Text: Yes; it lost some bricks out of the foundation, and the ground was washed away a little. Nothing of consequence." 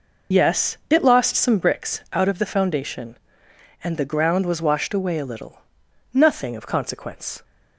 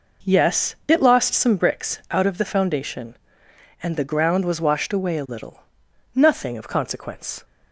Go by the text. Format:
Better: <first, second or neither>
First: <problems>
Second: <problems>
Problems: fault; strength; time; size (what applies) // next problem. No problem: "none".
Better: second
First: loses the start of "Yes"; at 0.3 s; 80 ms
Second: none